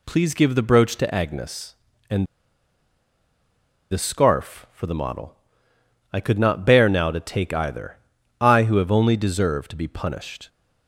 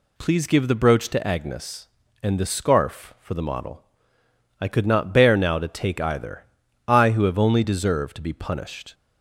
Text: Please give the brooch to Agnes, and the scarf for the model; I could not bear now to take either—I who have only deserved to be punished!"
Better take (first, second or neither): second